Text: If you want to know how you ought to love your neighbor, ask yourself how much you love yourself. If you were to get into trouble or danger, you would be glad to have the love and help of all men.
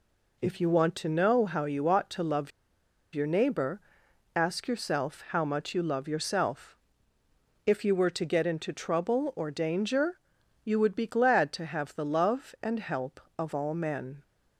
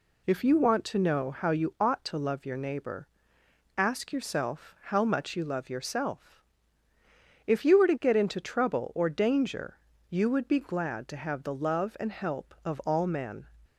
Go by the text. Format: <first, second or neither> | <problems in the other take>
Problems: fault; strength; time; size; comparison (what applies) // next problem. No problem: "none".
second | pauses between "love" and "your"; noticeable; at 2.5 s; 0.63 s long